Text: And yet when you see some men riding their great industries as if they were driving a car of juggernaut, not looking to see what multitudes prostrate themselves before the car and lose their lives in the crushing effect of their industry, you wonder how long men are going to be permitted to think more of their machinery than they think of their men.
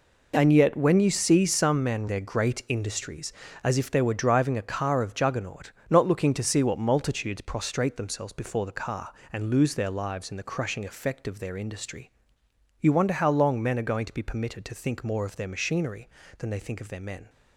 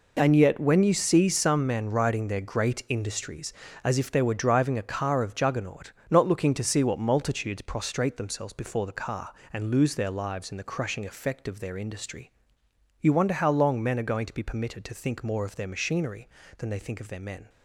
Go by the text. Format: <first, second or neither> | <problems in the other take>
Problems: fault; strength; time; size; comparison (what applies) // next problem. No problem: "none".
second | skips "riding"; at 2.0 s